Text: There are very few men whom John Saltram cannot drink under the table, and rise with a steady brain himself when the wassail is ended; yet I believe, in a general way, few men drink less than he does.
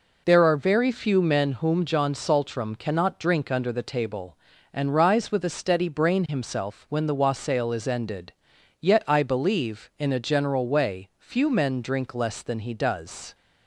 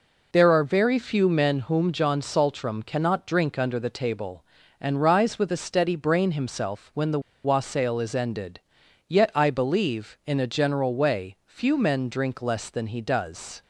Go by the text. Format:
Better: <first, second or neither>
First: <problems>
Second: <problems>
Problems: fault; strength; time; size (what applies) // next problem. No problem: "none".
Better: first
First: none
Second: pauses between "the" and "wassail"; slight; at 7.1 s; 0.25 s long